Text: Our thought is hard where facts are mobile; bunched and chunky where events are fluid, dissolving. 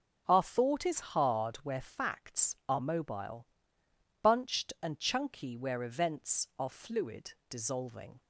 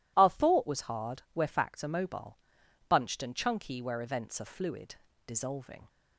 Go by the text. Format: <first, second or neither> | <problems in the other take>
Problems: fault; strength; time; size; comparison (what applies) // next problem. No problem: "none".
first | says "was" for "is"; at 0.6 s